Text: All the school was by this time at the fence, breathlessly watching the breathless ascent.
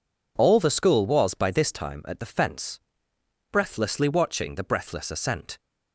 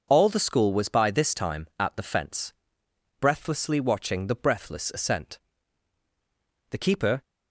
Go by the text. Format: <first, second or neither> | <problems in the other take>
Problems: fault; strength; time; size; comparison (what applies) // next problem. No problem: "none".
first | goes on to say "The keeper"; from 6.7 s on; 0.52 s long